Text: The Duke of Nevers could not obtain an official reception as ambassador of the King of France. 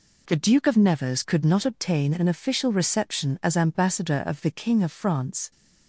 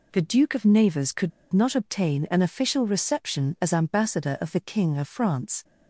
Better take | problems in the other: first | pauses between "could" and "not"; slight; at 1.3 s; 0.22 s long

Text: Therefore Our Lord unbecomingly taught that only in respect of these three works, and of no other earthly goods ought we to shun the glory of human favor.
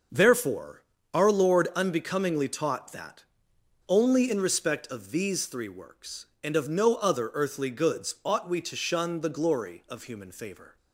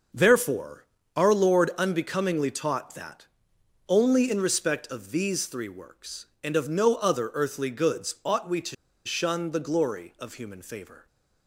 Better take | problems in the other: first | starts louder than the rest; noticeable; until 1.4 s; 6 dB; noticeable in the first // pauses between "Therefore" and "Our"; slight; at 0.8 s; 0.32 s long; slight in the first // pauses between "that" and "only"; noticeable; at 3.2 s; 0.62 s long; noticeable in the first // pauses between "to" and "shun"; slight; at 8.7 s; 0.31 s long

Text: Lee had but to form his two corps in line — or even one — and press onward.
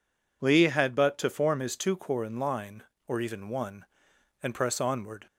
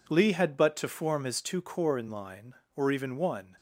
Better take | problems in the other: first | stops before "and press onward"; at 3.5 s

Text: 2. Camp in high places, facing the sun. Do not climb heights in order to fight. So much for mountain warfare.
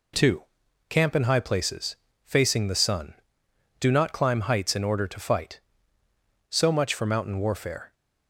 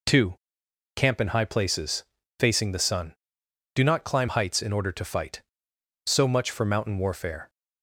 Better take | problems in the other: neither | none

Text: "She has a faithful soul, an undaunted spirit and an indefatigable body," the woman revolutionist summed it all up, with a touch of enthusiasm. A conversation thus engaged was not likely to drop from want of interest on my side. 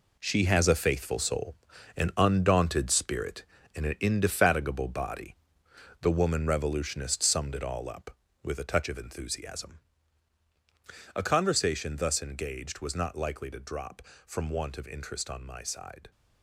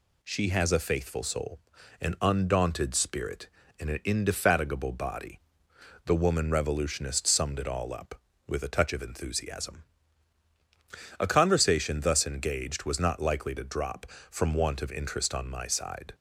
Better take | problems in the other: second | gets quieter; strong; throughout; 10.5 dB

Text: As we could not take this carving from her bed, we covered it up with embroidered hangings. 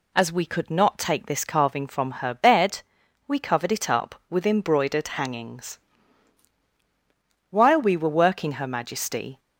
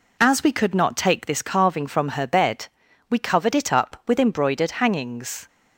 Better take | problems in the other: second | goes on to say "While we were working Her Majesty"; strong; from 7.4 s on; 1.9 s long

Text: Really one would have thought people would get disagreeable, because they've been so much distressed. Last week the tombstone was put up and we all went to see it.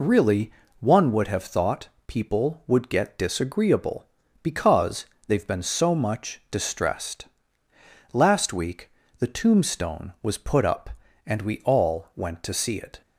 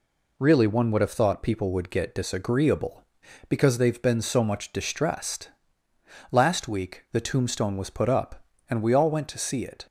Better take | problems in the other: second | loses the start of "Really"; at 0.0 s; 25 ms // pauses between "Really" and "one"; slight; at 0.5 s; 0.26 s long // pauses between "thought" and "people"; slight; at 1.8 s; 0.18 s long // pauses between "because" and "they've"; slight; at 5.0 s; 0.22 s long // pauses between "week" and "the"; slight; at 8.8 s; 0.30 s long

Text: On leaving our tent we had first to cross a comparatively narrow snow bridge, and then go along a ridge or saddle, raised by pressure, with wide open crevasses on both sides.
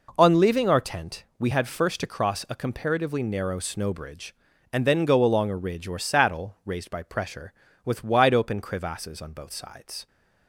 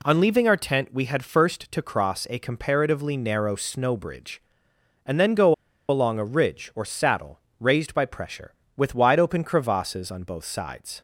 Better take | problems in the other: first | pauses between "go" and "along"; slight; at 5.5 s; 0.34 s long

